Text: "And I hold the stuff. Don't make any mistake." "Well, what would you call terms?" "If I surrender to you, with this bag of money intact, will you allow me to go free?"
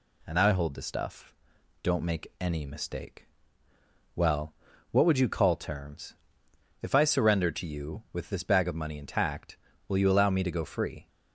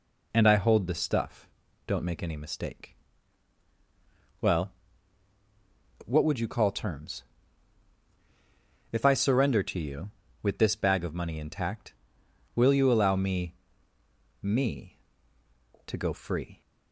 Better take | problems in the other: first | says "me" twice; at 14.4 s

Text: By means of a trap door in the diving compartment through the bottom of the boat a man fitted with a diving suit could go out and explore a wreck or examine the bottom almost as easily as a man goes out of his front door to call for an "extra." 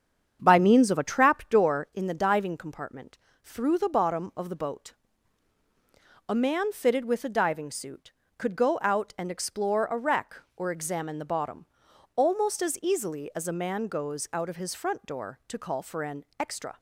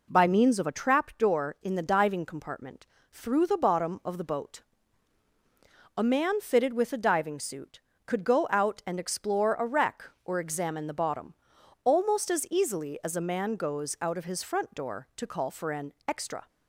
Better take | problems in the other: second | starts louder than the rest; strong; until 2.1 s; 8 dB // pauses between "compartment" and "through"; slight; at 3.1 s; 0.26 s long; slight in the second // pauses between "boat" and "a"; strong; at 4.9 s; 1.3 s long; strong in the second // pauses between "bottom" and "almost"; noticeable; at 11.6 s; 0.48 s long; noticeable in the second

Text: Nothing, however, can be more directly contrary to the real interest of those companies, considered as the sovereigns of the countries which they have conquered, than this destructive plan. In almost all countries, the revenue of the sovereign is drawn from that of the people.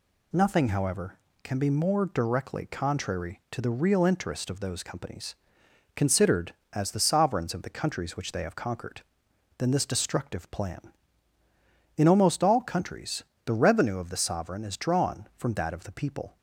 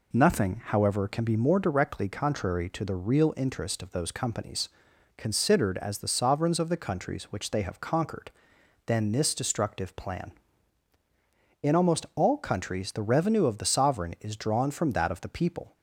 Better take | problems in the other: neither | none

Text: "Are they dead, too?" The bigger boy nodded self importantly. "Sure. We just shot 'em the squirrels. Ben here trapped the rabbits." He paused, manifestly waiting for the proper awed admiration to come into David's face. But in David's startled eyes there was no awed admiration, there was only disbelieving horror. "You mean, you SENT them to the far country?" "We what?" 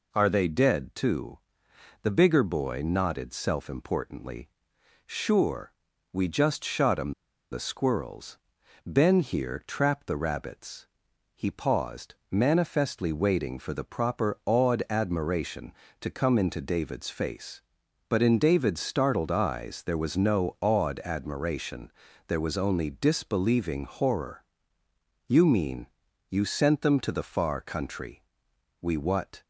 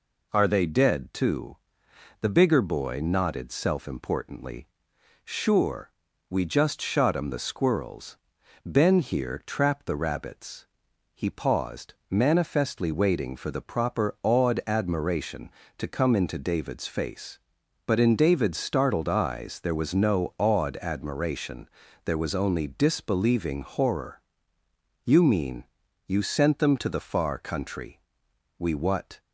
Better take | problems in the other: second | pauses between "em" and "the"; at 7.1 s; 0.39 s long

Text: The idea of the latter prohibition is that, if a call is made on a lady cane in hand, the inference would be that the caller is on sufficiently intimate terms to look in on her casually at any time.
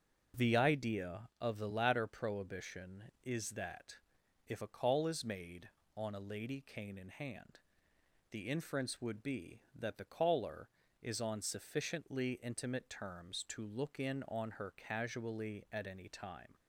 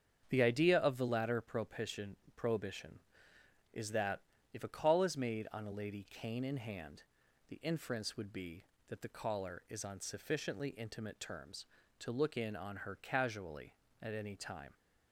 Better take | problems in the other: first | starts louder than the rest; strong; until 1.3 s; 7.5 dB // says "prohibition" twice; at 2.3 s

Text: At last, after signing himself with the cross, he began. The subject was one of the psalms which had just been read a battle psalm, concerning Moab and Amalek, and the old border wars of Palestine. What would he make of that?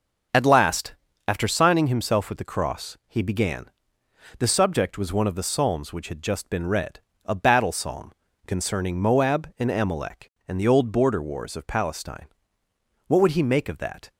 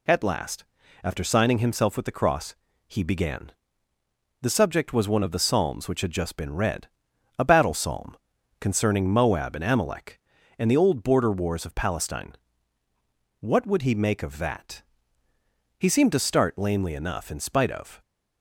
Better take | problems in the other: first | pauses between "read" and "a"; noticeable; at 6.8 s; 0.52 s long; slight in the first // goes on to say "He seemed to start lamely enough in spite of"; strong; from 15.7 s on; 2.2 s long

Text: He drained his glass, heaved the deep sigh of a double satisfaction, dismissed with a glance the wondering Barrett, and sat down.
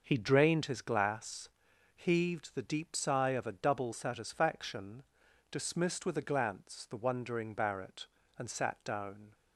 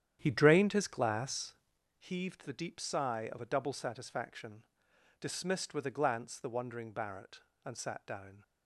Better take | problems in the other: first | starts louder than the rest; strong; until 1.9 s; 10 dB

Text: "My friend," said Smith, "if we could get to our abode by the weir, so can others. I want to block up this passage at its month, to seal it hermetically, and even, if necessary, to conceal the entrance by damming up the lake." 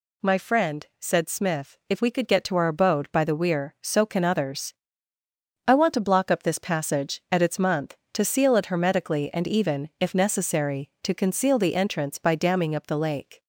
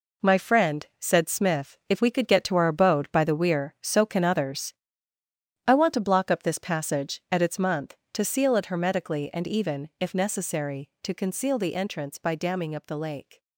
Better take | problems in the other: first | gets quieter; strong; throughout; 9.5 dB

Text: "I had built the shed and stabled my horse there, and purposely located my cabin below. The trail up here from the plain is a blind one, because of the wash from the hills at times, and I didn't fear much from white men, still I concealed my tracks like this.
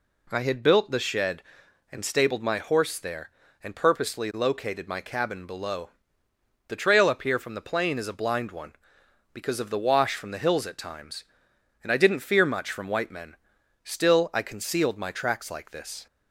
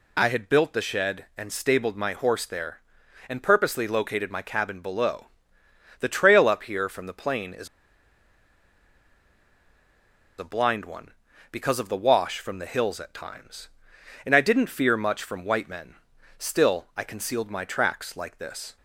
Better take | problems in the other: first | pauses between "is" and "a"; strong; at 7.6 s; 2.7 s long

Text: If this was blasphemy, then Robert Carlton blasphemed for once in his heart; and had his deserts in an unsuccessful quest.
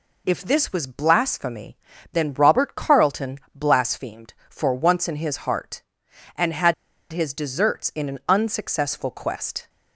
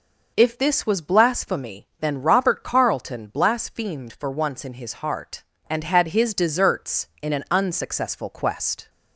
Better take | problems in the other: second | pauses between "Carlton" and "blasphemed"; slight; at 3.3 s; 0.16 s long // pauses between "had" and "his"; at 6.7 s; 0.38 s long

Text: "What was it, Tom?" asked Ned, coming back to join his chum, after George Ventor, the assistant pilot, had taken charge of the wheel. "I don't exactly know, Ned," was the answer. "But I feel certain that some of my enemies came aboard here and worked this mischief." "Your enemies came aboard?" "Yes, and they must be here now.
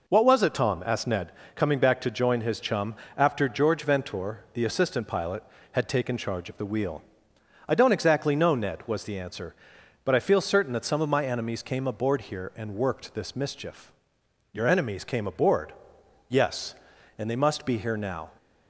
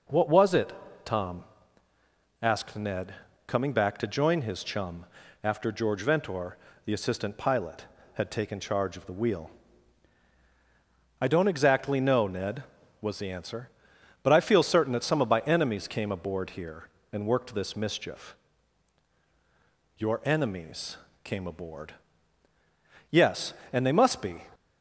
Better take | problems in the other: first | pauses between "enemies" and "came"; slight; at 20.9 s; 0.28 s long // stops before "here now"; at 24.5 s

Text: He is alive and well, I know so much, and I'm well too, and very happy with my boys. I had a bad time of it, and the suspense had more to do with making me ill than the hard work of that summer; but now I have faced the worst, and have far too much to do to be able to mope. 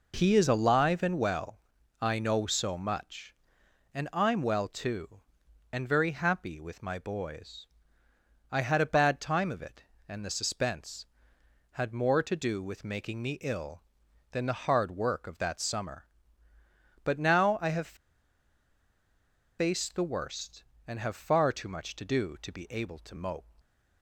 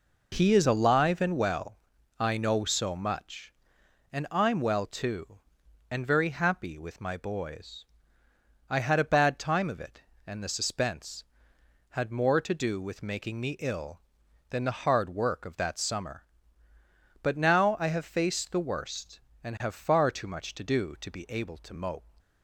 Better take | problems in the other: second | pauses between "have" and "faced"; strong; at 17.9 s; 1.6 s long

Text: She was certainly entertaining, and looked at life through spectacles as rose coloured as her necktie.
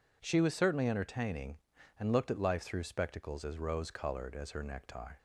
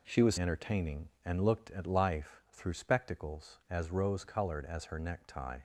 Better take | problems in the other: first | skips "certainly"; at 0.3 s

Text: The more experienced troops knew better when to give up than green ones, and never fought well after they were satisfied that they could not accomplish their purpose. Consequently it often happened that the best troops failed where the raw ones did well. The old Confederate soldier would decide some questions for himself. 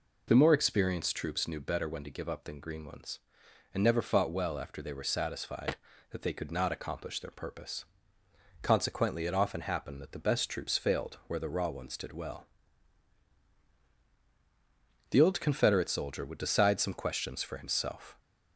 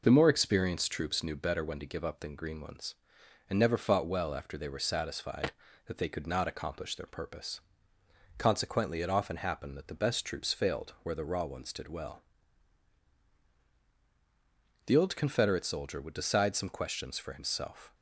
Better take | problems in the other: first | gets quieter; slight; throughout; 2 dB

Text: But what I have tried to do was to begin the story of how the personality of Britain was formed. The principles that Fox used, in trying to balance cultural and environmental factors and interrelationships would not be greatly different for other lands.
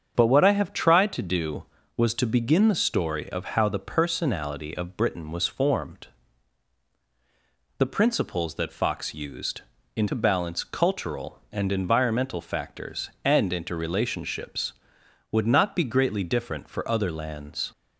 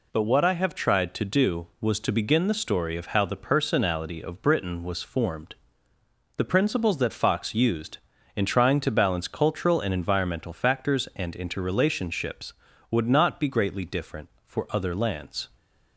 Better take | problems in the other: second | starts louder than the rest; strong; until 1.1 s; 7.5 dB // skips "trying"; at 10.0 s

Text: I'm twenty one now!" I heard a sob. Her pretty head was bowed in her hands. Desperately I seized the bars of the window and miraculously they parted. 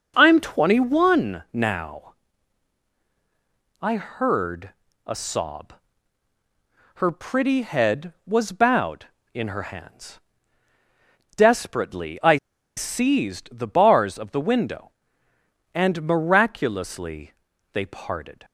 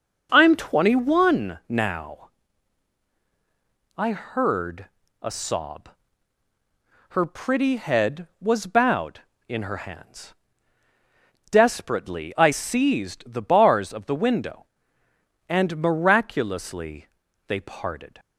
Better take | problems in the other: second | starts louder than the rest; noticeable; until 1.1 s; 6 dB; noticeable in the second // pauses between "heard" and "a"; slight; at 4.7 s; 0.34 s long; slight in the second // pauses between "I" and "seized"; at 12.3 s; 0.40 s long // pauses between "miraculously" and "they"; at 17.3 s; 0.40 s long; also in the second

